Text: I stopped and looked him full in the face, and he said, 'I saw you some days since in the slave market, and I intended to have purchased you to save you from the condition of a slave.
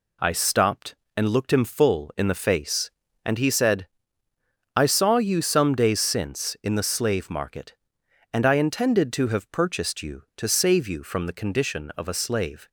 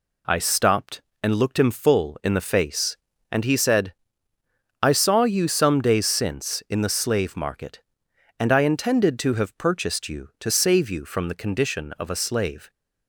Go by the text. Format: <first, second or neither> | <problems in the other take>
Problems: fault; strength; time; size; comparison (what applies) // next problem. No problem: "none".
neither | none